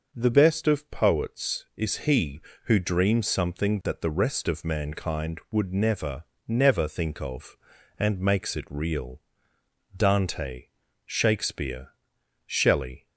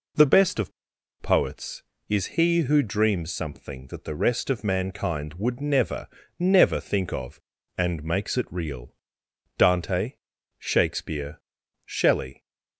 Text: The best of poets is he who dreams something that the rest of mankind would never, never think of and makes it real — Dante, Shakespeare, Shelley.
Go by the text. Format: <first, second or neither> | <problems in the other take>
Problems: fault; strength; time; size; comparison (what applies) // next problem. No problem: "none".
first | pauses between "of" and "poets"; noticeable; at 0.7 s; 0.50 s long